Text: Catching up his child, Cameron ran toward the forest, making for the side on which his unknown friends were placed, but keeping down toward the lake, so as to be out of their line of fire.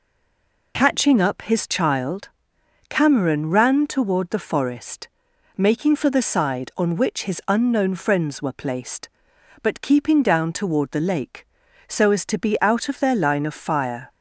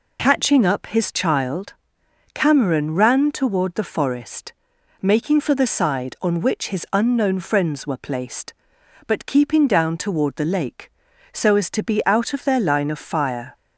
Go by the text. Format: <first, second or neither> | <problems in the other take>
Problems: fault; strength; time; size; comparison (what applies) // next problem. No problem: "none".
second | stays silent before the first word; slight; until 0.7 s; 0.7 s long